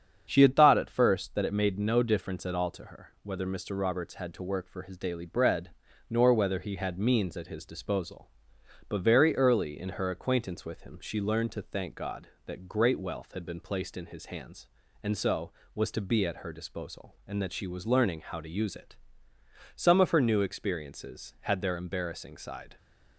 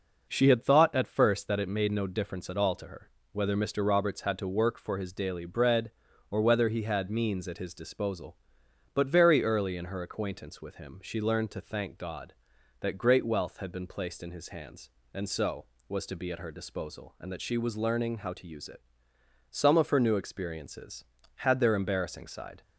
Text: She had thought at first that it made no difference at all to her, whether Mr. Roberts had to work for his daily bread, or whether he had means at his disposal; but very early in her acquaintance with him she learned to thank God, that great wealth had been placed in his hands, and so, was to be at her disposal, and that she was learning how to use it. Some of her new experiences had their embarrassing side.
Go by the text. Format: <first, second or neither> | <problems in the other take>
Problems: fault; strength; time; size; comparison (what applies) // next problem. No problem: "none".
second | starts louder than the rest; strong; until 1.2 s; 7.5 dB // says "nor" for "or"; at 6.1 s